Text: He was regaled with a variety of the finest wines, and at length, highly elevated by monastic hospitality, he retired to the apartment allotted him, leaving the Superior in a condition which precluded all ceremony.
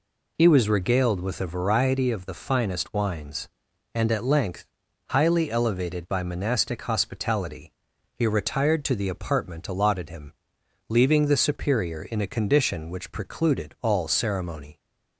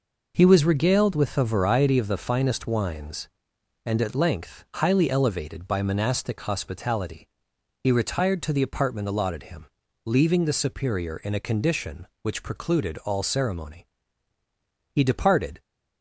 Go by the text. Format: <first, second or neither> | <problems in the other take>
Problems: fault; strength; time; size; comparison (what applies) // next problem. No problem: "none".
first | goes on to say "He departed"; noticeable; from 14.9 s on; 0.70 s long